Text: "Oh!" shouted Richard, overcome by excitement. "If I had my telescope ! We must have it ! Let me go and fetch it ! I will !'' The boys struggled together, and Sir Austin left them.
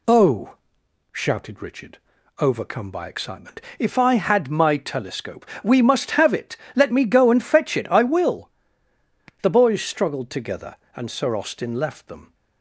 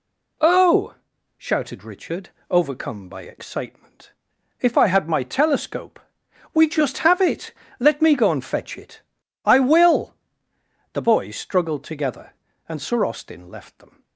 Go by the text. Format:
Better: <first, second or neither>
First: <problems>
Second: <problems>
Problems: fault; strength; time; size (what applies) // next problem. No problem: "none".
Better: first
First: none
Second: says "just" for "must"; at 6.6 s